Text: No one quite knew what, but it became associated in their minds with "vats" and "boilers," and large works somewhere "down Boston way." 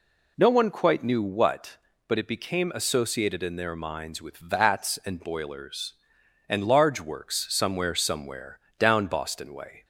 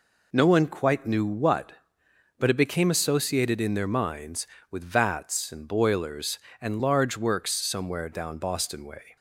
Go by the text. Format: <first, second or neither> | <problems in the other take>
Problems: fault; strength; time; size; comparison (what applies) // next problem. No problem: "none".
second | says "somewhere" twice; at 7.9 s